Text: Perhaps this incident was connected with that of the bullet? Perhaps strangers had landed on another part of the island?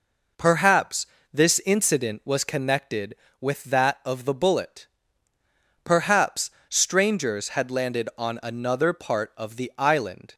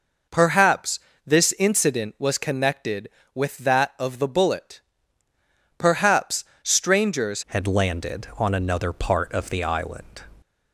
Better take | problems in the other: first | pauses between "Perhaps" and "this"; slight; at 0.9 s; 0.26 s long; slight in the first // pauses between "Perhaps" and "strangers"; slight; at 6.4 s; 0.18 s long; slight in the first // changes voice at "had"; from 7.4 s on; 2.8 s long

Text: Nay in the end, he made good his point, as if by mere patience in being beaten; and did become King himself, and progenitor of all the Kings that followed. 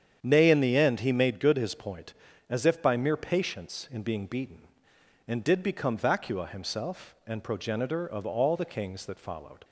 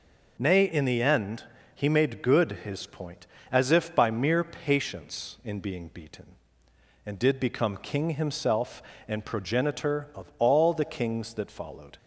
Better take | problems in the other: second | starts louder than the rest; strong; until 1.2 s; 8.5 dB // says "Vacua" for "King"; at 5.9 s

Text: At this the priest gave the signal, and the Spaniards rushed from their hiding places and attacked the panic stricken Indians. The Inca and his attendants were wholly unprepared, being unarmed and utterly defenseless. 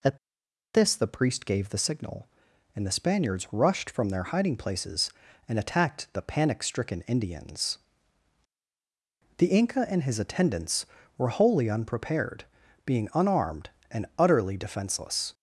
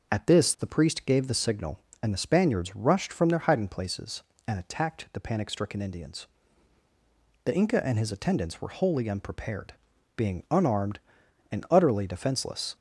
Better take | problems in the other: second | pauses between "At" and "this"; noticeable; at 0.1 s; 0.56 s long

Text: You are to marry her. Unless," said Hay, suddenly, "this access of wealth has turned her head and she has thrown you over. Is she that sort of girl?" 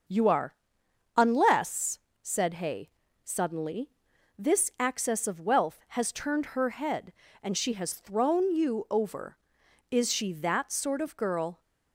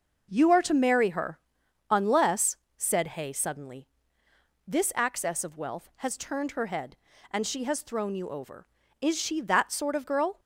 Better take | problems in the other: second | starts louder than the rest; until 1.7 s; 6.5 dB // skips "to marry her"; at 0.8 s

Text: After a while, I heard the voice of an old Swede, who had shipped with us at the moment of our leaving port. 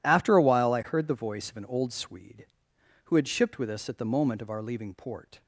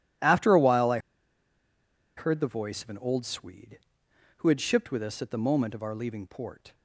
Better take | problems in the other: first | pauses between "I" and "heard"; at 0.9 s; 1.1 s long

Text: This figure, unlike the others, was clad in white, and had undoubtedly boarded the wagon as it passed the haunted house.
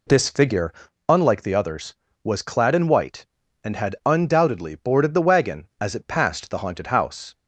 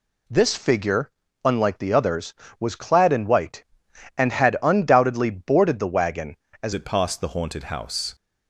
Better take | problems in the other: first | changes voice at "it"; from 6.7 s on; 1.4 s long

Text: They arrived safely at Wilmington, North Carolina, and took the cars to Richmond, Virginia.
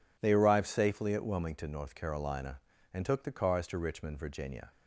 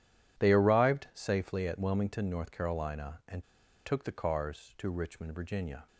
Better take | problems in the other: first | pauses between "and" and "took"; at 3.4 s; 0.43 s long

